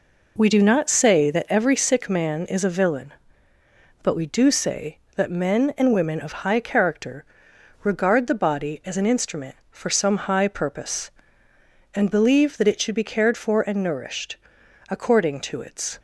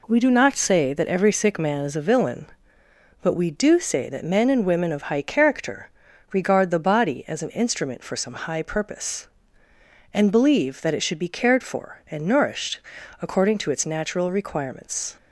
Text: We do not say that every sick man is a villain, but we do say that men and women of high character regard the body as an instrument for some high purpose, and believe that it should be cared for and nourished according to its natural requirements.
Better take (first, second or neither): second